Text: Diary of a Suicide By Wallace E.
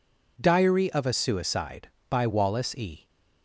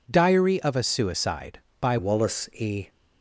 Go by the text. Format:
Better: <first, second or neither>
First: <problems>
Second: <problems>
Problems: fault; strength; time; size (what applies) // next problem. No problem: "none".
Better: first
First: none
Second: changes voice at "Wallace"; from 1.9 s on; 0.9 s long